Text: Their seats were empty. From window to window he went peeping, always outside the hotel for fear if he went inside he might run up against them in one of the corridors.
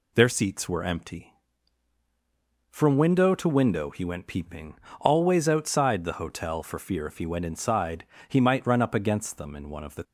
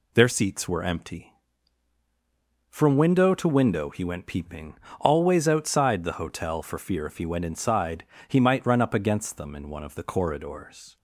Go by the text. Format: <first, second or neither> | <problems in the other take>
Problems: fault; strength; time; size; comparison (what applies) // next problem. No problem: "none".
second | pauses between "inside" and "he"; slight; at 8.0 s; 0.22 s long; slight in the second // stops before "corridors"; at 10.0 s